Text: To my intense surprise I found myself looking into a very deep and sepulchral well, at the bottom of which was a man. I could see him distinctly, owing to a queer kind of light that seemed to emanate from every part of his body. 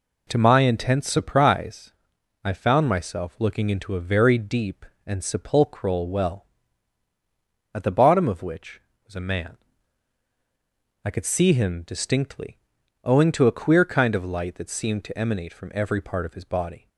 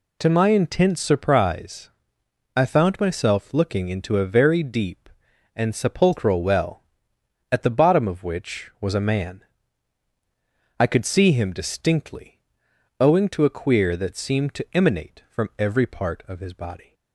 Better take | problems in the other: first | pauses between "surprise" and "I"; noticeable; at 1.8 s; 0.66 s long; noticeable in the first // skips "kind of light"; at 13.9 s

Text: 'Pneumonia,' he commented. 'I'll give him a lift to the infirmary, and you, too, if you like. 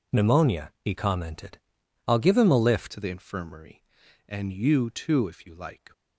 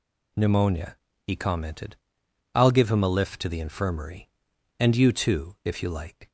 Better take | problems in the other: second | changes voice at "to"; from 2.9 s on; 3.0 s long

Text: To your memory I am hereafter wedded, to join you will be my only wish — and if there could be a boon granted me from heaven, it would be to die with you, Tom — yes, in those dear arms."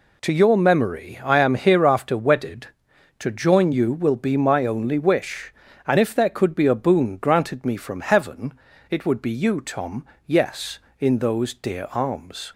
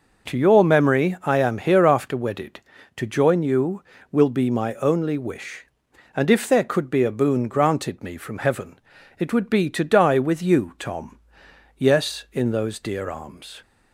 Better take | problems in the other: second | skips "to die with"; at 9.3 s

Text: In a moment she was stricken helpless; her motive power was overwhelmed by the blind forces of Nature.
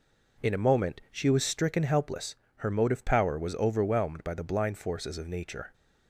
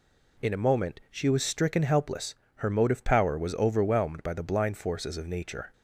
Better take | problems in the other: second | starts louder than the rest; noticeable; until 1.6 s; 4.5 dB

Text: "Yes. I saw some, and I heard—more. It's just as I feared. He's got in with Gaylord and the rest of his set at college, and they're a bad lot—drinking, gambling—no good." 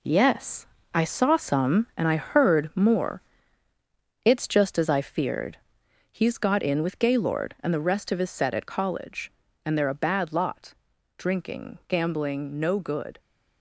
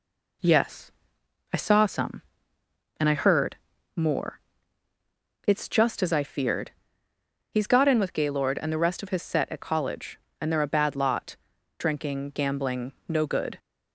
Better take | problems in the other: second | gets quieter; noticeable; throughout; 5.5 dB

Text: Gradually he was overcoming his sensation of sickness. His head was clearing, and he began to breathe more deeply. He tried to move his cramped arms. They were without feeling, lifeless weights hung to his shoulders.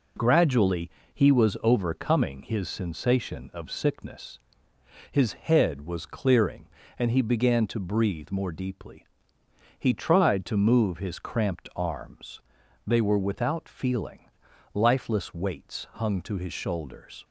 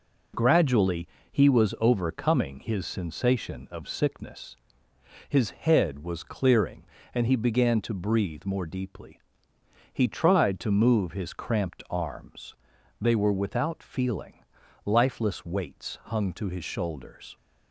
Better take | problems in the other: neither | pauses between "Gradually" and "he"; slight; the same in both

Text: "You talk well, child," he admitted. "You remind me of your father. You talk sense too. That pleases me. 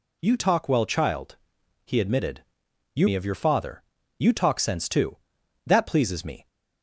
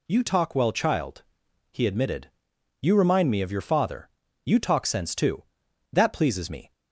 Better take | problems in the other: second | skips "remind"; at 3.0 s

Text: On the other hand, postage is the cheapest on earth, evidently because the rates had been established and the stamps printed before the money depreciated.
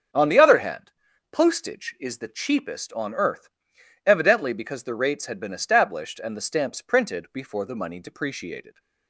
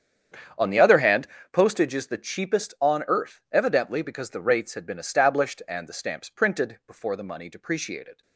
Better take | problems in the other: first | gets quieter; strong; throughout; 16.5 dB // starts louder than the rest; strong; until 1.8 s; 8 dB; strong in the first

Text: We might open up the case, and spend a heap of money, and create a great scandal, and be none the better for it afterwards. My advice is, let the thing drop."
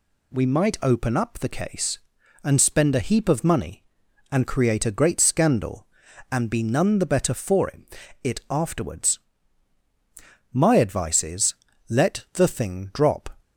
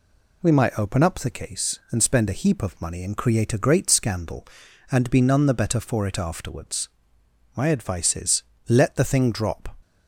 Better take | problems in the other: second | says "it" twice; at 8.2 s

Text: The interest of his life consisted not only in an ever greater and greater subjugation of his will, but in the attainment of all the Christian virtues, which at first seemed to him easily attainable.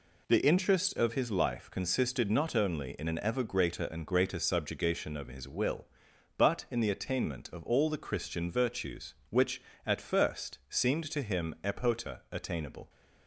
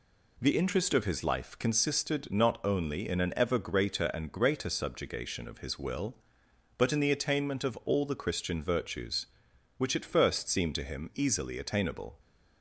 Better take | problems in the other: second | says "epota" for "easily"; at 11.6 s

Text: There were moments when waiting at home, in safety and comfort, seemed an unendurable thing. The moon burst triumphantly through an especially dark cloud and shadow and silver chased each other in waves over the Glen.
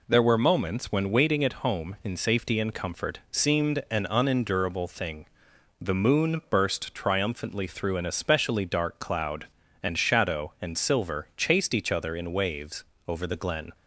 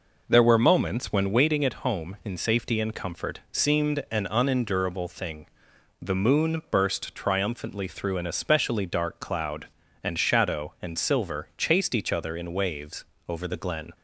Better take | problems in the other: first | starts louder than the rest; noticeable; until 1.4 s; 5 dB // pauses between "waves" and "over"; slight; at 13.0 s; 0.24 s long; slight in the first

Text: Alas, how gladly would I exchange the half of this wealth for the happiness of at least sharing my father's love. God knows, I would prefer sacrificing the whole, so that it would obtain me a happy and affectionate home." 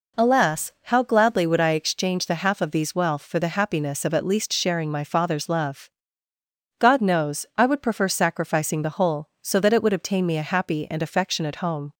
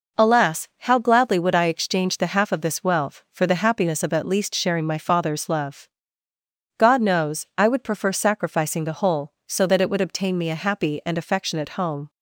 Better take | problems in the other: second | says "these" for "this"; at 2.6 s

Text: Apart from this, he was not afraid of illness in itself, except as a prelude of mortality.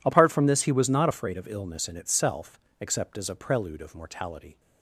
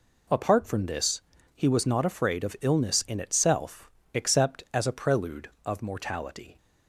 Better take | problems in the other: neither | none

